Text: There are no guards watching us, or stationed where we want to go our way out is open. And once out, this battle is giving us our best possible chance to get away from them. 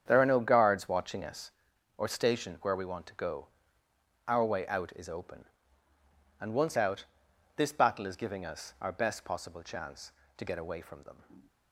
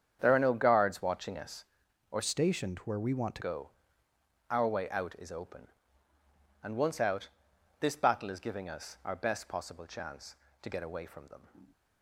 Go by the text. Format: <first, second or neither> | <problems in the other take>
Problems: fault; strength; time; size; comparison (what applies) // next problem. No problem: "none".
first | starts louder than the rest; strong; until 1.2 s; 8 dB; strong in the first // changes voice from "stationed" to "to"; from 2.2 to 3.4 s; 1.2 s long // pauses between "go" and "our"; noticeable; at 3.6 s; 0.82 s long; noticeable in the first